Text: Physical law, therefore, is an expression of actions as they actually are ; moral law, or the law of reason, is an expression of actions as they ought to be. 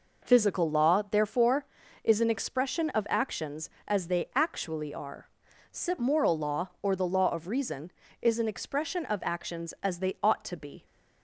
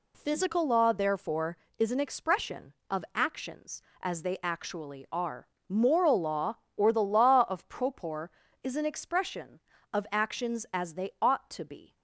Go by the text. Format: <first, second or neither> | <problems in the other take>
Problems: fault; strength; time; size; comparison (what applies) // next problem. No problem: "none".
first | says "propor" for "reason"; at 7.6 s